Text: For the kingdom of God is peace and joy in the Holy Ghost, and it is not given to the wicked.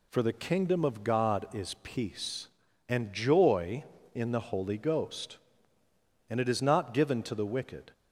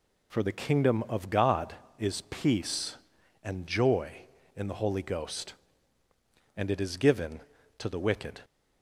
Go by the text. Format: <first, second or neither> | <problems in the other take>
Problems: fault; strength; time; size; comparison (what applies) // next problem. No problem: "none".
first | skips "not"; at 6.9 s